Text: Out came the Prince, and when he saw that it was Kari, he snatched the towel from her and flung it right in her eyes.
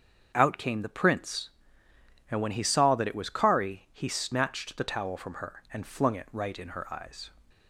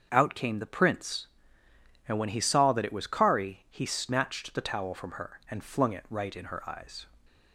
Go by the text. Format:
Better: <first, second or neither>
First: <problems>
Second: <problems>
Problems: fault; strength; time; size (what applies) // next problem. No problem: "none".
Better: neither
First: starts louder than the rest; strong; until 1.3 s; 7 dB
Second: starts louder than the rest; until 1.1 s; 7 dB